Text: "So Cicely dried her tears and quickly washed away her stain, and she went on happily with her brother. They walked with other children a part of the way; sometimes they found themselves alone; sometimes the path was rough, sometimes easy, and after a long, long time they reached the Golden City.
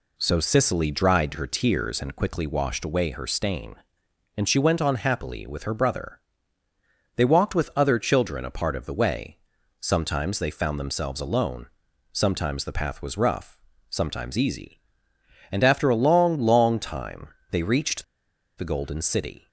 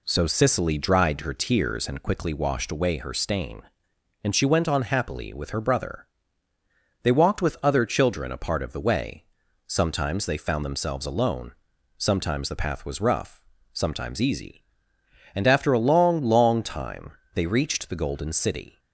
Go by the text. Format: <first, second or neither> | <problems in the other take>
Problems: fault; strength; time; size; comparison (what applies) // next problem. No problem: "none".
second | pauses between "time" and "they"; slight; at 17.2 s; 0.22 s long; slight in the second // pauses between "reached" and "the"; noticeable; at 18.0 s; 0.55 s long